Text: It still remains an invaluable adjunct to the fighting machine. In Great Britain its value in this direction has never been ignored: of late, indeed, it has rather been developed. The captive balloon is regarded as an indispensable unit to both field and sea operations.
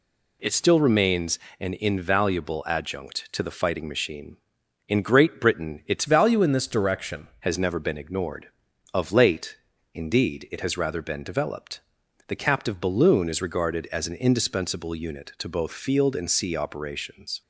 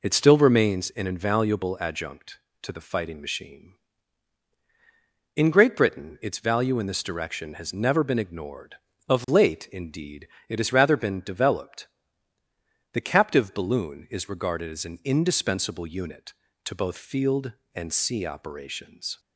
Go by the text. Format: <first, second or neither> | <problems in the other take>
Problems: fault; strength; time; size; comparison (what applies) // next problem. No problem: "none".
second | pauses between "remains" and "an"; slight; at 1.3 s; 0.22 s long // changes voice from "value" to "direction"; from 6.0 to 7.2 s; 1.2 s long